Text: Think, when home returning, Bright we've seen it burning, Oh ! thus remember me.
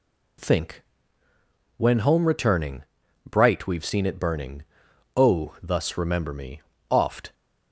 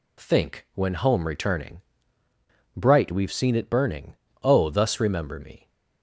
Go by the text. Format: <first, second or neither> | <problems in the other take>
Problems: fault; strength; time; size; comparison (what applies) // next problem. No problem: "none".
second | goes on to say "Oft"; slight; from 6.8 s on; 0.44 s long